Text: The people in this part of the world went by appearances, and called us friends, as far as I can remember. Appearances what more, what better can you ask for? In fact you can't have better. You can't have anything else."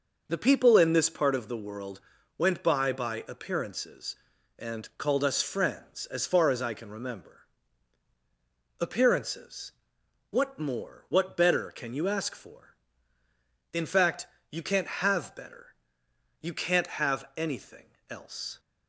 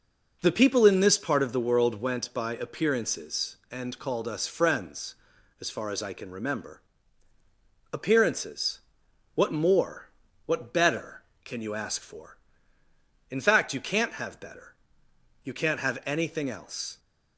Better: second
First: pauses between "world" and "went"; at 1.9 s; 0.38 s long // says "by" twice; at 2.9 s // pauses between "Appearances" and "what"; noticeable; at 9.7 s; 0.58 s long // pauses between "fact" and "you"; slight; at 14.2 s; 0.24 s long // pauses between "anything" and "else"; slight; at 17.8 s; 0.22 s long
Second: pauses between "Appearances" and "what"; noticeable; at 8.7 s; 0.54 s long

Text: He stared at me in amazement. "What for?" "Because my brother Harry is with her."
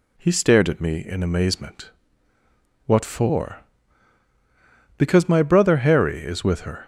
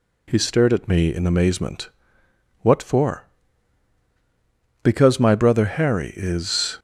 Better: first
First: none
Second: stops before "with her"; at 6.7 s

